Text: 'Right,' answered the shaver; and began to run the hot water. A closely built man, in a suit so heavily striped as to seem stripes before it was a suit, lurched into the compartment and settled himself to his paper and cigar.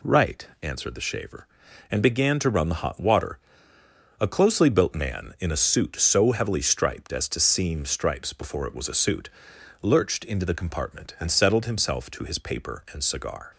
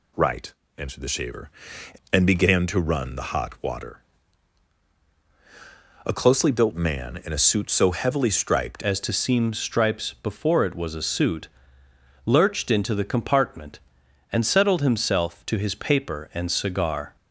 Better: first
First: none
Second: changes voice at "as"; from 8.8 s on; 8.3 s long

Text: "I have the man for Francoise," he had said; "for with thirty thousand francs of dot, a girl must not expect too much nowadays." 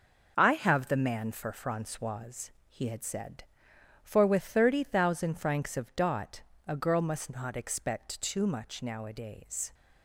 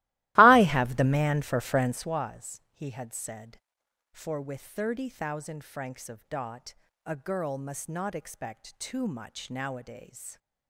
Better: first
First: none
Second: starts louder than the rest; strong; until 2.2 s; 17.5 dB

